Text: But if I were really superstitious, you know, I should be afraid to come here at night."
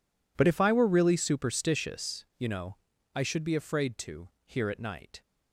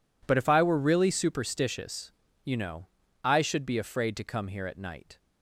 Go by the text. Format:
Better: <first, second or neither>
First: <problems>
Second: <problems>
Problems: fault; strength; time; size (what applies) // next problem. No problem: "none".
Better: second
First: skips "come"; at 4.3 s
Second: none